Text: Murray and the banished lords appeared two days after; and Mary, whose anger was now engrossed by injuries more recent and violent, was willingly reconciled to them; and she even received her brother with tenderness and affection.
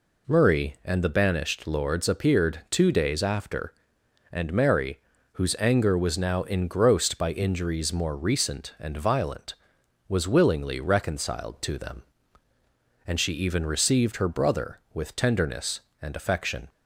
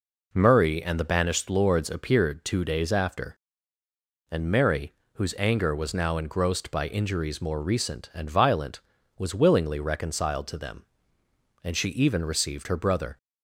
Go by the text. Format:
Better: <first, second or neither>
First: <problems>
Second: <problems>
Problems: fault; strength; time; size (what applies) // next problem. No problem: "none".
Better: first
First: none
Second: stops before "with tenderness and affection"; at 13.1 s